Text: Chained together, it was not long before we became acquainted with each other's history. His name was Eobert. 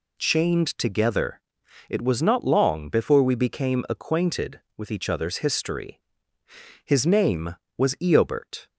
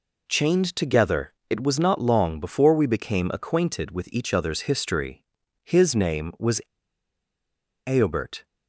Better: first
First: none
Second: pauses between "was" and "Eobert"; strong; at 6.5 s; 1.2 s long

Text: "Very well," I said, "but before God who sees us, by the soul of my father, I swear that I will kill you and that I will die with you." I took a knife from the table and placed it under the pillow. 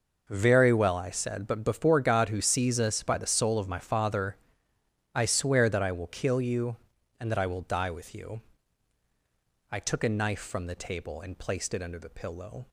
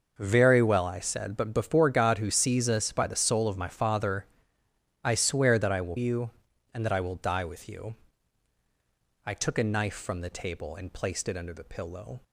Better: first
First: none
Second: skips "kill"; at 5.9 s

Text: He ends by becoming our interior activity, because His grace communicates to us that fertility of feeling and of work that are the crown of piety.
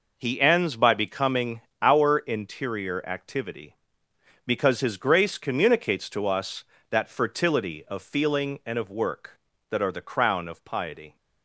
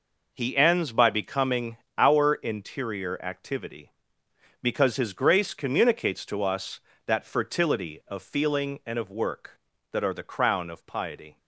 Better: neither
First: pauses between "becoming" and "our"; slight; at 1.6 s; 0.18 s long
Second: pauses between "becoming" and "our"; slight; at 1.7 s; 0.18 s long

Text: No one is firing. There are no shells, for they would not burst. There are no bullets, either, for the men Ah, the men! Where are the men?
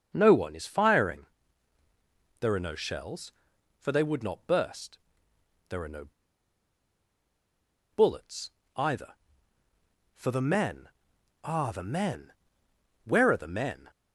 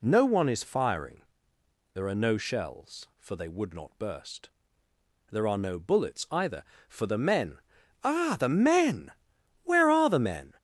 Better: second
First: starts louder than the rest; until 1.1 s; 6.5 dB // pauses between "no" and "bullets"; strong; at 6.0 s; 1.8 s long // pauses between "men" and "Ah"; noticeable; at 10.8 s; 0.60 s long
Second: pauses between "men" and "Ah"; noticeable; at 7.5 s; 0.46 s long

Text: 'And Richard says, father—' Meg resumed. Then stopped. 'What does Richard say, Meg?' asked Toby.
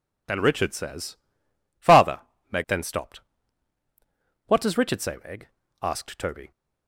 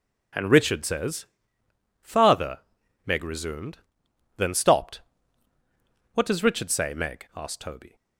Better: second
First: skips "resumed"; at 2.6 s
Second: none

